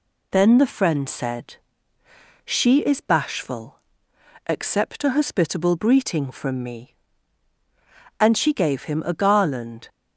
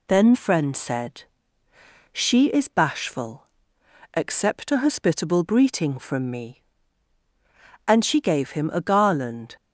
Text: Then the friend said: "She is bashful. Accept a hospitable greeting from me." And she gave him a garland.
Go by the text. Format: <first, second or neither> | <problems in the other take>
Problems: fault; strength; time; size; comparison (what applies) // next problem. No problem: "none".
first | skips "the"; at 0.3 s